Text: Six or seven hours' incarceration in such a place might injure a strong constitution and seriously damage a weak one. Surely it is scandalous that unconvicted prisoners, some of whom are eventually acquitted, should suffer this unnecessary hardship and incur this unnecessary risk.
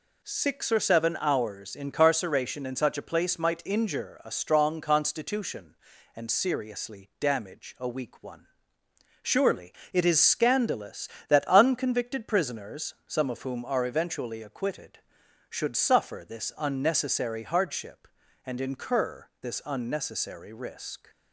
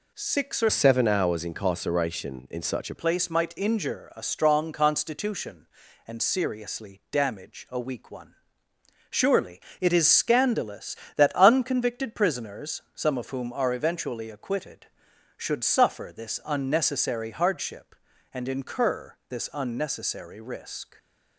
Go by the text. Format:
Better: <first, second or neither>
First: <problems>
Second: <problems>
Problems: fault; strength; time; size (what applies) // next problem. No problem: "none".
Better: first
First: pauses between "Surely" and "it"; slight; at 9.7 s; 0.22 s long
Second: changes voice from "seven" to "a"; from 0.6 to 2.9 s; 2.3 s long // pauses between "Surely" and "it"; slight; at 9.5 s; 0.22 s long